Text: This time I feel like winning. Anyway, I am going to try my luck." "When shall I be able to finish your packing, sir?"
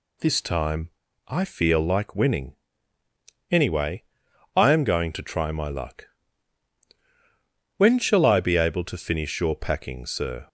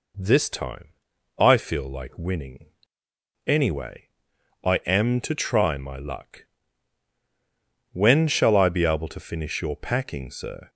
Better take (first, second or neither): first